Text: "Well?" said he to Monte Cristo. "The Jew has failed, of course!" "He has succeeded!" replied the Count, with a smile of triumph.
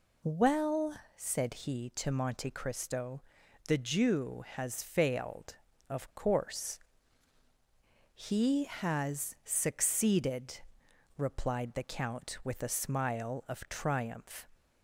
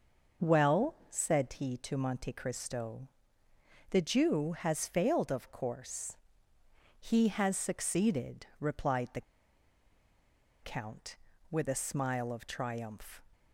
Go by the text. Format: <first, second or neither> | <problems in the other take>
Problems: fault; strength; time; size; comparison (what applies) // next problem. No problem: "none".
first | pauses between "the" and "Count"; strong; at 9.2 s; 1.4 s long